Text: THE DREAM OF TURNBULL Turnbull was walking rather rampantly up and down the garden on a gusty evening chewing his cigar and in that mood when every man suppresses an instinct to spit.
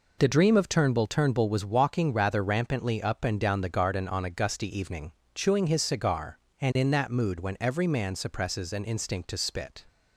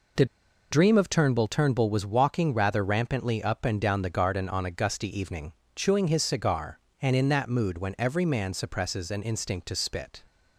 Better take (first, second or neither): first